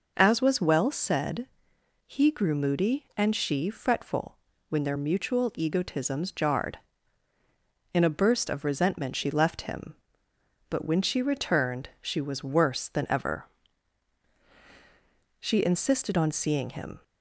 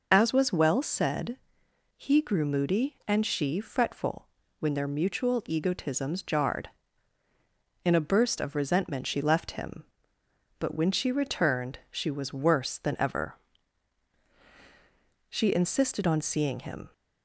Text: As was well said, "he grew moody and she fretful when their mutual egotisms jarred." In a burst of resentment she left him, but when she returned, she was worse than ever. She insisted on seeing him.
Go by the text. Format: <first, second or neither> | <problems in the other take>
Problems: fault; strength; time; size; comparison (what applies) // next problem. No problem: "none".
first | loses the start of "As"; at 0.1 s; 45 ms // pauses between "fretful" and "when"; slight; at 4.2 s; 0.32 s long; slight in the first